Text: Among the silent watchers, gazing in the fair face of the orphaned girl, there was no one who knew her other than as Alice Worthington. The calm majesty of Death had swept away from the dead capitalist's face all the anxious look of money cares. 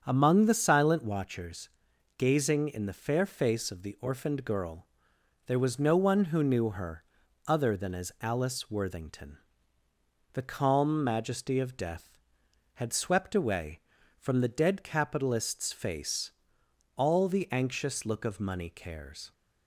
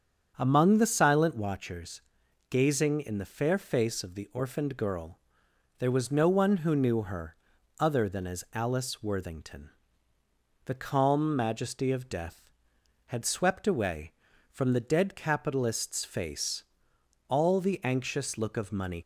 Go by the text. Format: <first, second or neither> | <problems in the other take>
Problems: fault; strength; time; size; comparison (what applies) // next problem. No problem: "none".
first | starts louder than the rest; strong; until 1.3 s; 8 dB; strong in the first // pauses between "her" and "other"; at 7.3 s; 0.42 s long; also in the first // pauses between "face" and "all"; noticeable; at 16.6 s; 0.64 s long; noticeable in the first // stops before "cares"; at 19.0 s